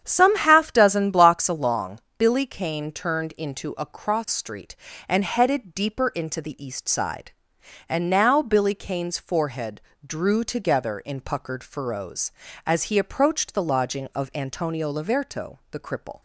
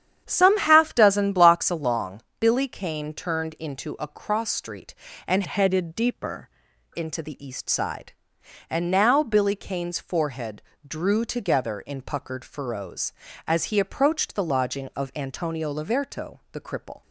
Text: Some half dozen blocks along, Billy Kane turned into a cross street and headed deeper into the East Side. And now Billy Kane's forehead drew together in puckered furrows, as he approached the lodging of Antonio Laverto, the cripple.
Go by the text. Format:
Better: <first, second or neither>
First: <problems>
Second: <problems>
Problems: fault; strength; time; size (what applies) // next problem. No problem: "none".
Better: first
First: starts louder than the rest; strong; until 1.0 s; 8.5 dB // pauses between "forehead" and "drew"; slight; at 9.8 s; 0.24 s long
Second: starts louder than the rest; strong; until 1.2 s; 9 dB // changes voice from "headed" to "deeper"; from 5.4 to 6.4 s; 1.0 s long // pauses between "forehead" and "drew"; slight; at 10.6 s; 0.24 s long